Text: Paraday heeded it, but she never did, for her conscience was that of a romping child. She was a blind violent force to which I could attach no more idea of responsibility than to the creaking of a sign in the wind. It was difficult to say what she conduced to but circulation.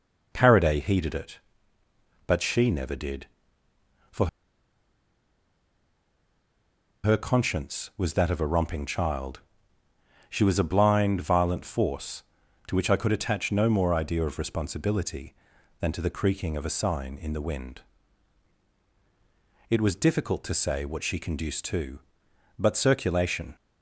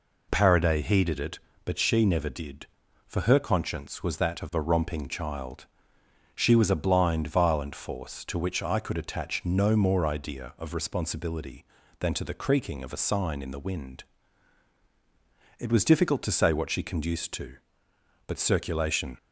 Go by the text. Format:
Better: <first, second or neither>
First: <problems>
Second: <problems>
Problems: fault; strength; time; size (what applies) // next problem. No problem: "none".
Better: second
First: pauses between "for" and "her"; strong; at 4.2 s; 2.7 s long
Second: none